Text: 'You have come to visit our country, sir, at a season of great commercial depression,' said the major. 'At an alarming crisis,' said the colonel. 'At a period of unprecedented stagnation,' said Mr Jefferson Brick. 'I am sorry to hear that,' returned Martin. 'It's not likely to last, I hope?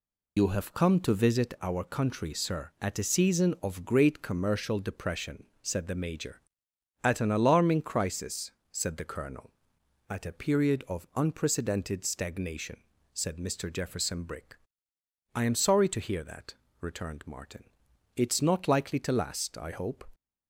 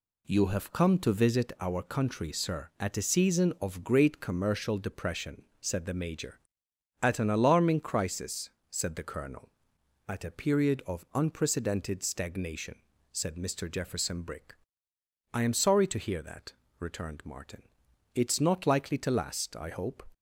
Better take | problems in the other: second | loses the start of "You"; at 0.3 s; 85 ms

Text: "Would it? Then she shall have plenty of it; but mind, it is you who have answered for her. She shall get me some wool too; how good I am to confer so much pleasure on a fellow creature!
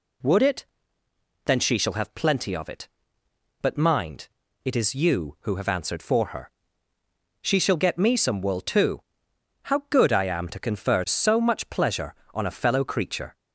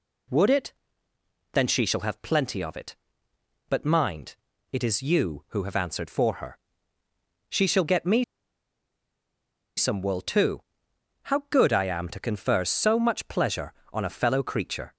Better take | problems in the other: first | pauses between "me" and "some"; strong; at 8.2 s; 1.5 s long

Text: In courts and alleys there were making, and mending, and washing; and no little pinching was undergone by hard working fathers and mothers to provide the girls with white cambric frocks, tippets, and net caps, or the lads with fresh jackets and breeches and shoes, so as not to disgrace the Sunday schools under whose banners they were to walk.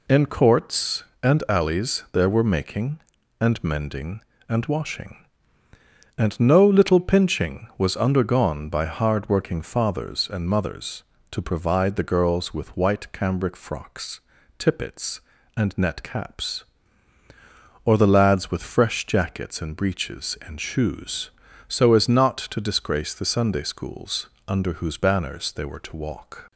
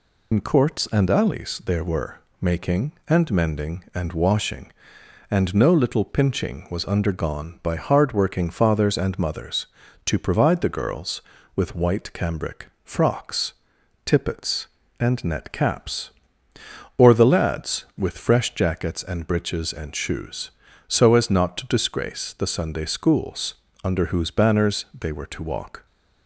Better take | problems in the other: first | loses the start of "In"; at 0.3 s; 75 ms // pauses between "were" and "making"; slight; at 2.2 s; 0.20 s long // pauses between "cambric" and "frocks"; slight; at 12.6 s; 0.16 s long // pauses between "schools" and "under"; slight; at 23.5 s; 0.32 s long; slight in the first // pauses between "banners" and "they"; slight; at 24.8 s; 0.16 s long

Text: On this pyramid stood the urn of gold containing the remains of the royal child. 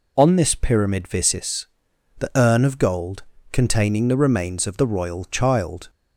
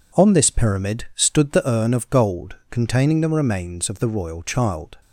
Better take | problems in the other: second | says "visis" for "stood"; at 1.0 s // pauses between "gold" and "containing"; slight; at 3.2 s; 0.30 s long

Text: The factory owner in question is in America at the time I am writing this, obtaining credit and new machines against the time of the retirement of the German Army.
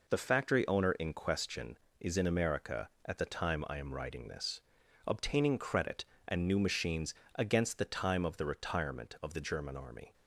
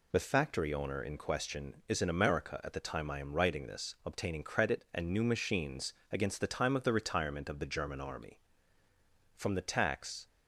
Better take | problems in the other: first | pauses between "machines" and "against"; slight; at 5.9 s; 0.18 s long; slight in the first // goes on to say "From the tax"; noticeable; from 9.3 s on; 0.90 s long

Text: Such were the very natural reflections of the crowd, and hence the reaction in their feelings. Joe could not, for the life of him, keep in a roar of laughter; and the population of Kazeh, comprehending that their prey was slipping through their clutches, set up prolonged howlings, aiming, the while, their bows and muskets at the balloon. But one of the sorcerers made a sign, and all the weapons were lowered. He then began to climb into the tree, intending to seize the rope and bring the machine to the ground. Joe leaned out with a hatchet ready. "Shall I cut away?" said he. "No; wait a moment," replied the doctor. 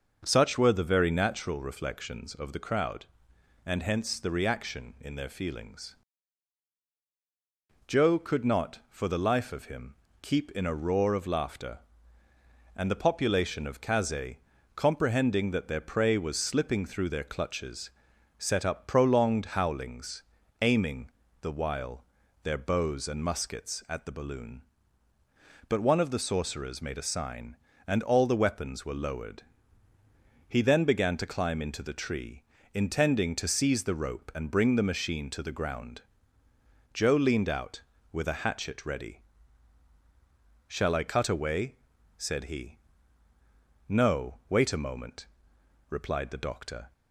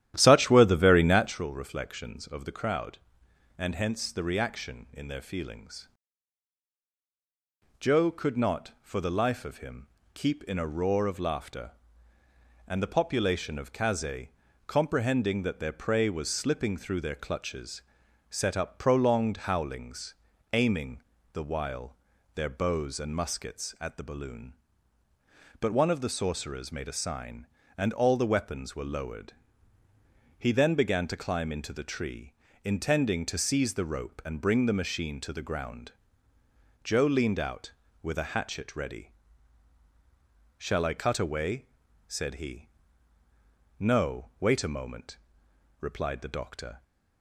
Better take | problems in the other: first | starts louder than the rest; strong; until 1.4 s; 12 dB

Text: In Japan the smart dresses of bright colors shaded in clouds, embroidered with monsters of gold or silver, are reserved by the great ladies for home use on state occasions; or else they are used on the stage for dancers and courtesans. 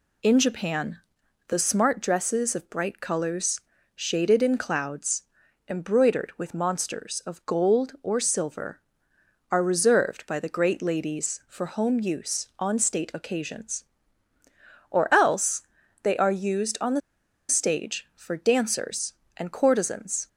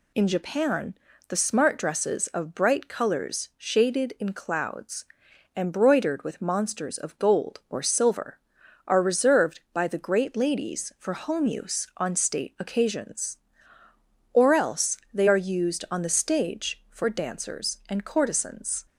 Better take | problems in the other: second | pauses between "Japan" and "the"; noticeable; at 0.9 s; 0.50 s long; slight in the second // pauses between "colors" and "shaded"; slight; at 3.6 s; 0.34 s long // pauses between "else" and "they"; at 15.6 s; 0.42 s long; slight in the second // pauses between "the" and "stage"; noticeable; at 17.0 s; 0.49 s long

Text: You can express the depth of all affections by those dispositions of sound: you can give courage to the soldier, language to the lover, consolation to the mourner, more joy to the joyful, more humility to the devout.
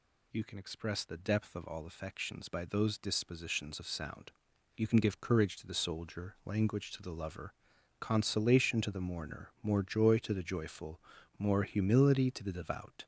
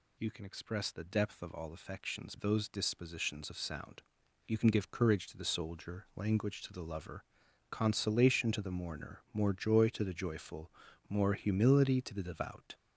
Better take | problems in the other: first | skips "by"; at 2.3 s

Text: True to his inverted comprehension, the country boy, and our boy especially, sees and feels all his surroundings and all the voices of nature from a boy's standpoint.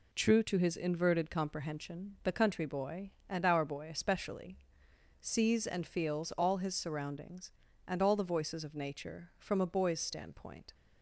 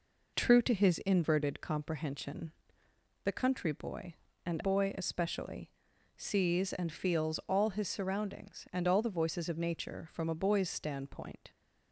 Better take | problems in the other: first | skips "our"; at 4.6 s

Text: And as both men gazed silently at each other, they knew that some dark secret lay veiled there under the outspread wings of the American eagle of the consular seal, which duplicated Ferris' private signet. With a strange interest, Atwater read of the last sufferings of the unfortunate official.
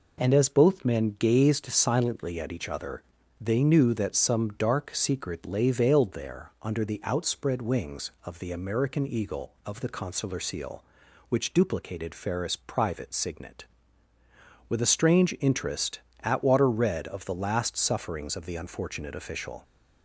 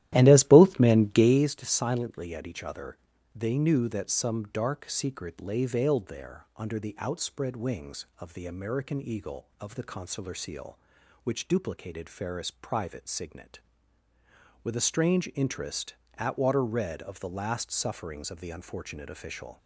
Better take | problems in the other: first | starts louder than the rest; strong; until 1.4 s; 13.5 dB

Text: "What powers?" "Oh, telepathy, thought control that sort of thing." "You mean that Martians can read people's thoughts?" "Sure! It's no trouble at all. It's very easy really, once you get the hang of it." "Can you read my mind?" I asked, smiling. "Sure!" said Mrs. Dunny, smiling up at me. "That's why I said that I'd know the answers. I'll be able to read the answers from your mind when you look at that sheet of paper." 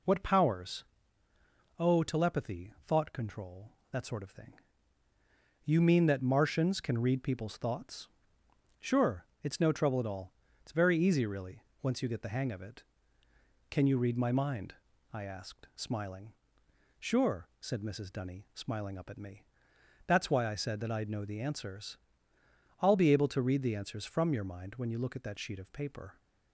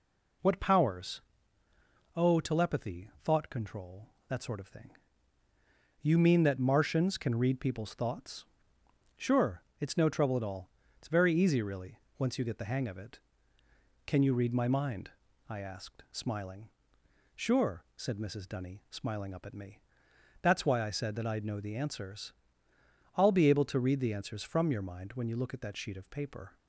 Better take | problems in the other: neither | none

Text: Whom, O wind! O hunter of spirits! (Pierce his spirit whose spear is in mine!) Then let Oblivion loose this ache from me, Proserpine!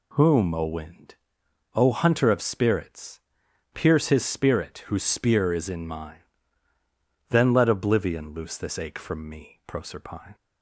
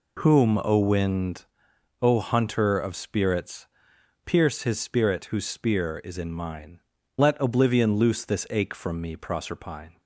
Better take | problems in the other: first | skips "Then"; at 6.9 s

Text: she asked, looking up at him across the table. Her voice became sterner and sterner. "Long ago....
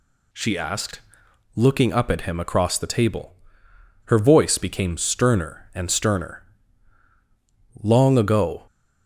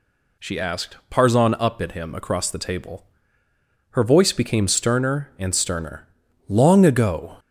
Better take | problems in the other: first | says "parzon" for "looking"; at 1.1 s

